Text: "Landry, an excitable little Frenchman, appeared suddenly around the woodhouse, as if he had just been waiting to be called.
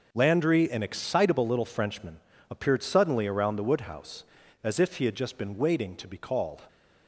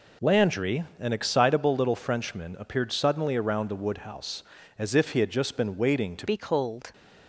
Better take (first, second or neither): first